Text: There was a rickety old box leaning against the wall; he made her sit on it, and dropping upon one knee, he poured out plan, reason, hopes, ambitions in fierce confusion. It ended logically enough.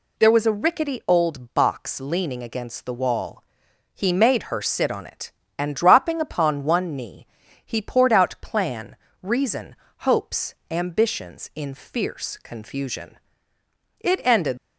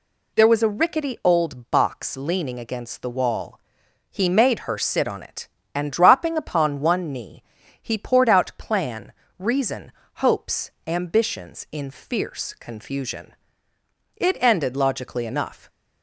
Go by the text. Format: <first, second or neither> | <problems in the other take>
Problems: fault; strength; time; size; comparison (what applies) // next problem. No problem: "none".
second | stops before "logically enough"; at 14.5 s